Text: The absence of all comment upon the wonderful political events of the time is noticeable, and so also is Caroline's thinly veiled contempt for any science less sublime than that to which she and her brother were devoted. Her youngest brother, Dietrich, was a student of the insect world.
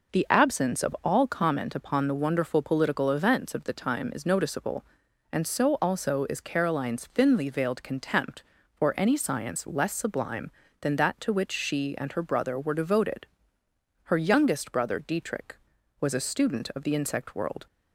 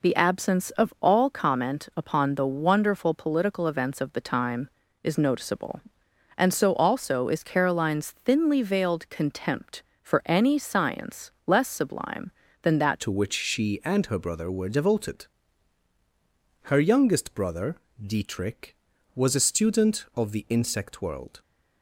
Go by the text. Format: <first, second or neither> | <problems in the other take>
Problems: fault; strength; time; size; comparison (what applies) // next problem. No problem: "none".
first | changes voice at "to"; from 13.0 s on; 8.4 s long